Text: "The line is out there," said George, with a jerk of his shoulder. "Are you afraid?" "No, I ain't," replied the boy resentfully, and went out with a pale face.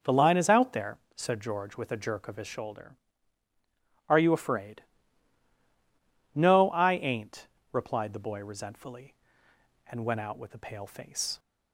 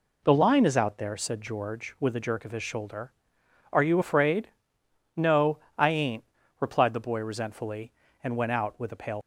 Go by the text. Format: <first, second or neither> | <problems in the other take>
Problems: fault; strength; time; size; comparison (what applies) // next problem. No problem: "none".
first | stops before "face"; at 9.2 s